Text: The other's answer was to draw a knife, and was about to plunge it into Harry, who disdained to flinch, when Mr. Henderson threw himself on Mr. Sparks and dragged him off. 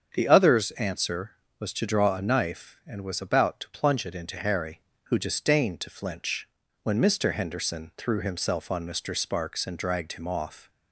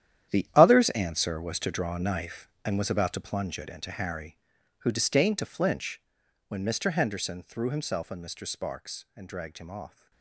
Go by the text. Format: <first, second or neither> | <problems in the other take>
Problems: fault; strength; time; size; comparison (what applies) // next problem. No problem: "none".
first | gets quieter; strong; throughout; 14.5 dB // starts louder than the rest; strong; until 1.4 s; 10.5 dB; strong in the first